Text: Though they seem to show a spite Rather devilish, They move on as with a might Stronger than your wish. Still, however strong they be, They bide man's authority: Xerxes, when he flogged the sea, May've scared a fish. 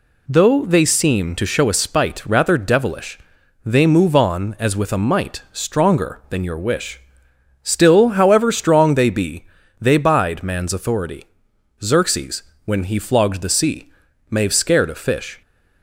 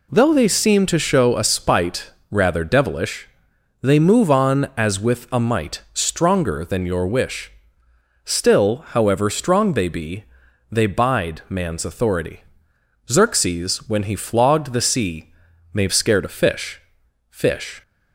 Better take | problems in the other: first | pauses between "spite" and "Rather"; slight; at 2.1 s; 0.20 s long // says "fish" twice; at 17.2 s

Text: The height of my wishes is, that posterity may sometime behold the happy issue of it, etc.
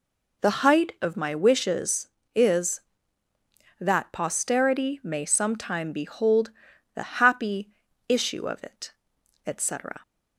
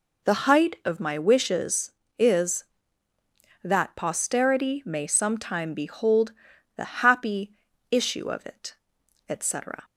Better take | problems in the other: neither | pauses between "behold" and "the"; the same in both // pauses between "happy" and "issue"; the same in both

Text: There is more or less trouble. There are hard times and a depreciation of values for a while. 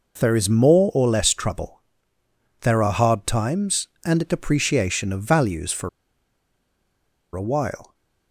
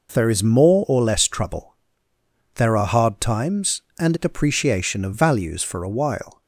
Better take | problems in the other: second | pauses between "for" and "a"; strong; at 5.8 s; 1.4 s long

